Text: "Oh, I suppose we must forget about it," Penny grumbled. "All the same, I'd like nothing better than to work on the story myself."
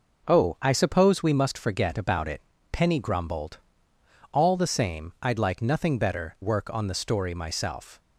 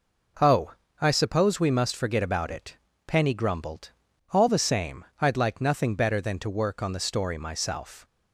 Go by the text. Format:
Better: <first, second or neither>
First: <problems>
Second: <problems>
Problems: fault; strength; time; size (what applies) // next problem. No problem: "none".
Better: second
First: skips "than to"; at 6.3 s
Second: none